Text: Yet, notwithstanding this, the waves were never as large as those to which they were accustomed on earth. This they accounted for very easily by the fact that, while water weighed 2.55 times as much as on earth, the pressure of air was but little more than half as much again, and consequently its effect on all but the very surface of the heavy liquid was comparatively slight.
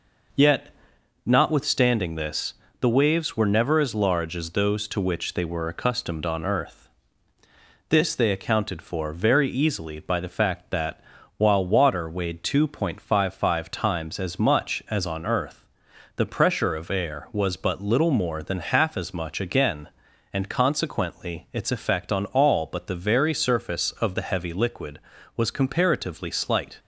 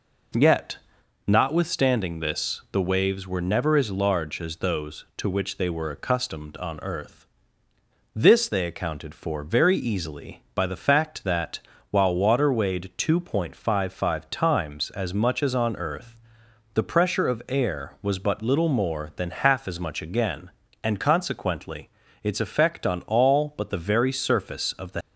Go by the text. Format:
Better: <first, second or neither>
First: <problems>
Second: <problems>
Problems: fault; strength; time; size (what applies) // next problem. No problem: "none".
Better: first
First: none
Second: pauses between "consequently" and "its"; slight; at 21.8 s; 0.34 s long // stops before "heavy liquid was comparatively slight"; at 25.0 s